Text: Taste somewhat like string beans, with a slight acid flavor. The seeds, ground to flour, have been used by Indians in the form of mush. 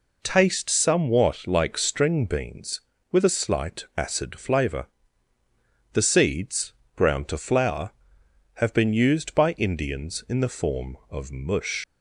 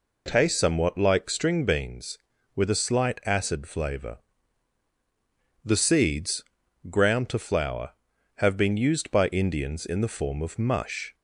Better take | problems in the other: second | leaves "mush" unfinished; at 11.8 s; 85 ms

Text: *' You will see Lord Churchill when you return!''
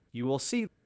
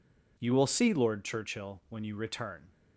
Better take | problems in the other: second | stops before "Lord Churchill when you return"; at 0.6 s

